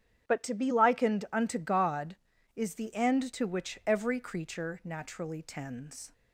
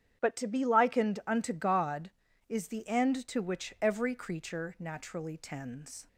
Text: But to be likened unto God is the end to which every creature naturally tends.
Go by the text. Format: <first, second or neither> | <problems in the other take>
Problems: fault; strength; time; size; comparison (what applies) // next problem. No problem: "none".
neither | starts louder than the rest; strong; the same in both